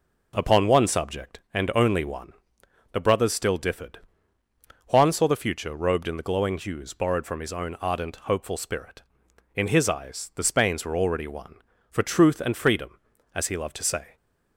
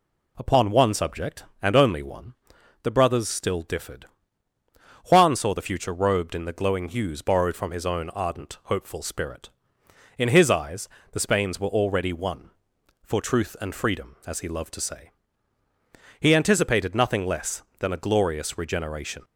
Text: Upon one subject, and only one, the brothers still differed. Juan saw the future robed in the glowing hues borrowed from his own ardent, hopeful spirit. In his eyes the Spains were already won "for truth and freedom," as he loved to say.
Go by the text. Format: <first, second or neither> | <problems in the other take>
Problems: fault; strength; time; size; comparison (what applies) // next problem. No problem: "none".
first | pauses between "eyes" and "the"; slight; at 10.8 s; 0.24 s long // goes on to say "He anticipated nothing less than a glorious regeneration"; strong; from 16.1 s on; 3.0 s long